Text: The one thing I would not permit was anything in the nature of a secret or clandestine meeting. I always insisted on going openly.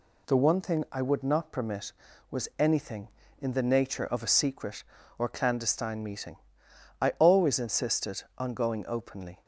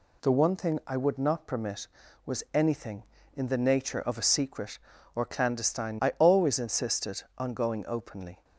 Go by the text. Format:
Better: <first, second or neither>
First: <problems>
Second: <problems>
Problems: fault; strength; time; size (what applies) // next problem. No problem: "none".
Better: first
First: none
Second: skips "meeting"; at 5.9 s